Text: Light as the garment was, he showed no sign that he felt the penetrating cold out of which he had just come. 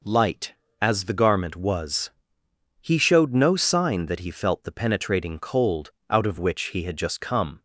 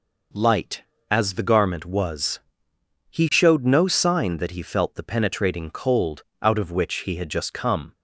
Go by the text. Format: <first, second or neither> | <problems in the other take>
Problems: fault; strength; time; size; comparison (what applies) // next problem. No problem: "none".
neither | pauses between "cold" and "out"; slight; the same in both